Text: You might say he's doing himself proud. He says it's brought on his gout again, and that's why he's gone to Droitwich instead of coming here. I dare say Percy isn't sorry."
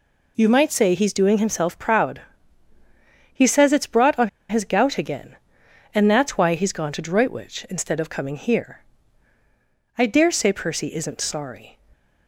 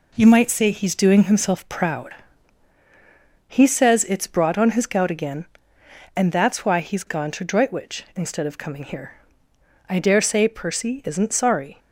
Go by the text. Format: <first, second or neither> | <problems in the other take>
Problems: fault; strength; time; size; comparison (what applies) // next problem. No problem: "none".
second | pauses between "on" and "his"; slight; at 4.2 s; 0.20 s long